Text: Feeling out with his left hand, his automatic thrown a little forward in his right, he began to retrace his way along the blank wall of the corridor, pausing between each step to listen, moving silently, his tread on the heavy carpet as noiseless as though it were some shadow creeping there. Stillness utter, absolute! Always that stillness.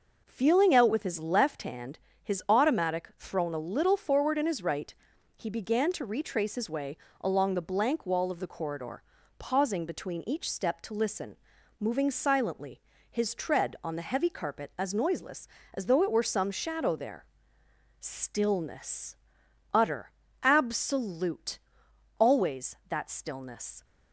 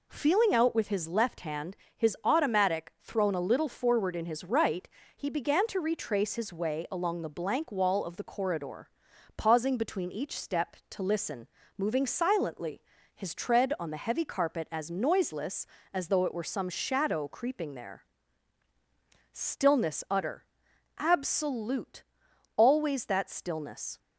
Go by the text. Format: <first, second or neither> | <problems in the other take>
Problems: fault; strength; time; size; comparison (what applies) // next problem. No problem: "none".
second | pauses between "way" and "along"; slight; at 6.9 s; 0.24 s long // skips "creeping"; at 16.9 s // pauses between "Stillness" and "utter"; noticeable; at 19.1 s; 0.58 s long